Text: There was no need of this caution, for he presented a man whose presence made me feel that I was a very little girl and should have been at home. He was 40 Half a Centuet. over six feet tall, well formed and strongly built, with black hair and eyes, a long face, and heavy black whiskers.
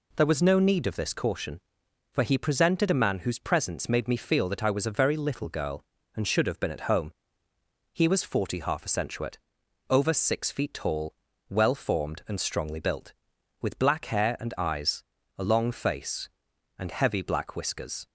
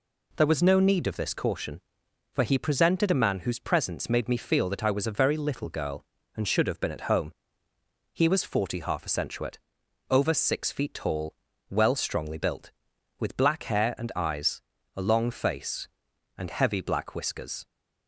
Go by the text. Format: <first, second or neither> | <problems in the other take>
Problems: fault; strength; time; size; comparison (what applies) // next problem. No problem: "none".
first | skips "formed and"; at 11.9 s